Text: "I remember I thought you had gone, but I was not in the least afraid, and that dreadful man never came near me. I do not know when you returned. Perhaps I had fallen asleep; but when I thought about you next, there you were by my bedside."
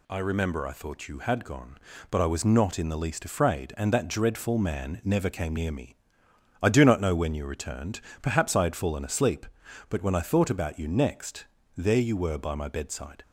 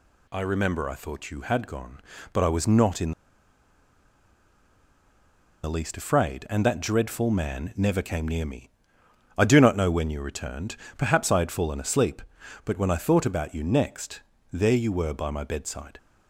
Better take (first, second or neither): first